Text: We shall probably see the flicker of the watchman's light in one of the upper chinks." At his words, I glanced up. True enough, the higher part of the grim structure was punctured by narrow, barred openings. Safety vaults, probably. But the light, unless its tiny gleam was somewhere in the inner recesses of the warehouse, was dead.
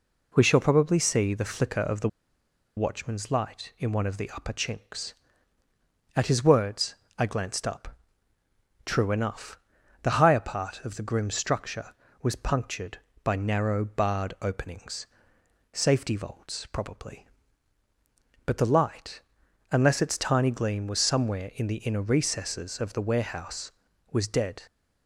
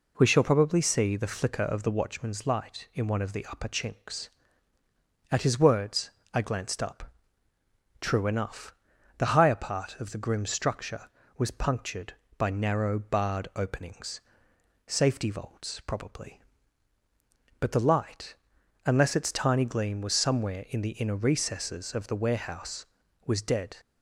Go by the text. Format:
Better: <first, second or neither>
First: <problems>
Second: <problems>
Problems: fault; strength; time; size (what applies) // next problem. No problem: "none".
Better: second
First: pauses between "the" and "watchman's"; noticeable; at 2.0 s; 0.69 s long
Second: none